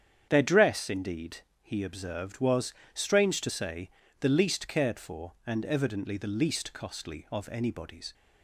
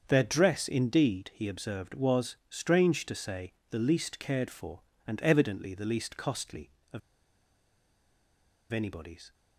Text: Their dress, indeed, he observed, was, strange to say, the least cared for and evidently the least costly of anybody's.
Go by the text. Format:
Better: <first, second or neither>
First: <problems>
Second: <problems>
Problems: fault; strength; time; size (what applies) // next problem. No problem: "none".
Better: first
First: starts louder than the rest; strong; until 1.3 s; 8.5 dB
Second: starts louder than the rest; until 1.0 s; 7 dB // pauses between "of" and "anybody's"; strong; at 7.0 s; 1.7 s long